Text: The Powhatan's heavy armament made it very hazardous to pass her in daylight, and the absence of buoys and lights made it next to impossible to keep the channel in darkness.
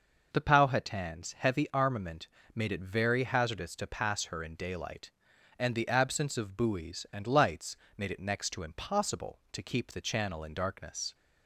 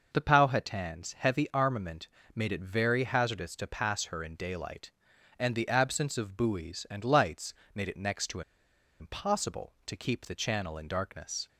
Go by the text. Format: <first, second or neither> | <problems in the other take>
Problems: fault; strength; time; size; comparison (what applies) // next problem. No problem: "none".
first | pauses between "armament" and "made"; slight; at 2.0 s; 0.26 s long; slight in the first // pauses between "lights" and "made"; slight; at 7.5 s; 0.20 s long; slight in the first // pauses between "to" and "impossible"; noticeable; at 8.4 s; 0.58 s long